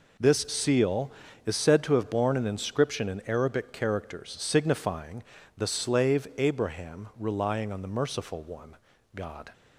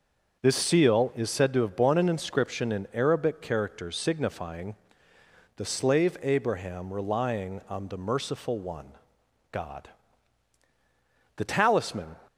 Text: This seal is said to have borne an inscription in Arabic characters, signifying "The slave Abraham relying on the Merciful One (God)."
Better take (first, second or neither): first